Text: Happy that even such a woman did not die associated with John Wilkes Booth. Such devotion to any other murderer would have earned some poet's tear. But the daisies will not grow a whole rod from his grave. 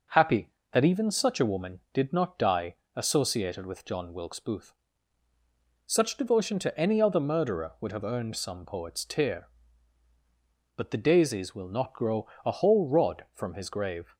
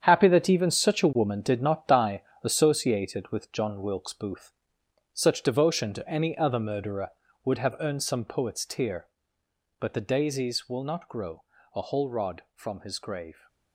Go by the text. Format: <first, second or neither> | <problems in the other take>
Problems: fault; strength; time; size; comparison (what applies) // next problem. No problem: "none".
first | gets quieter; strong; throughout; 10.5 dB // pauses between "die" and "associated"; slight; at 2.2 s; 0.20 s long; slight in the first // pauses between "grow" and "a"; slight; at 11.4 s; 0.30 s long; slight in the first